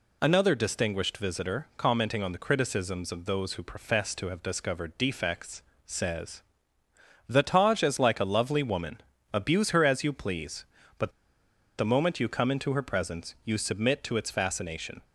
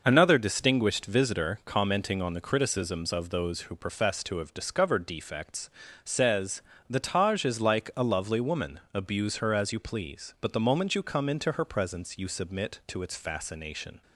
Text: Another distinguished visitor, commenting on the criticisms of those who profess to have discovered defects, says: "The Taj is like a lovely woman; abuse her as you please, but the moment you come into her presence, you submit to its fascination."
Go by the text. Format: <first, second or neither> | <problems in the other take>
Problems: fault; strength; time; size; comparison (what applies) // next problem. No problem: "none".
second | pauses between "but" and "the"; noticeable; at 11.1 s; 0.67 s long